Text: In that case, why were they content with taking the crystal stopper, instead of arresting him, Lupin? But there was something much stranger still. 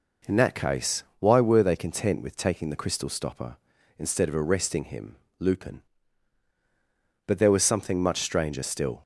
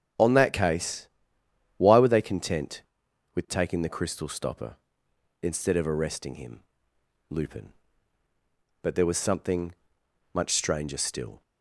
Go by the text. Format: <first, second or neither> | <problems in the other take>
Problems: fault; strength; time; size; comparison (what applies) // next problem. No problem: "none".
first | starts louder than the rest; strong; until 1.8 s; 7.5 dB // says "On" for "In"; at 0.1 s // pauses between "something" and "much"; noticeable; at 9.7 s; 0.58 s long